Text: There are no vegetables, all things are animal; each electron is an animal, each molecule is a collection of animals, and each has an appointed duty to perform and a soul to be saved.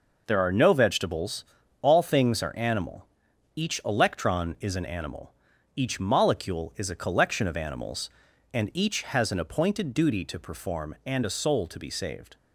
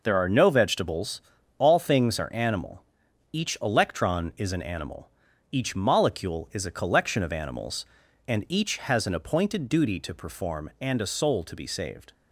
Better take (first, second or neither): neither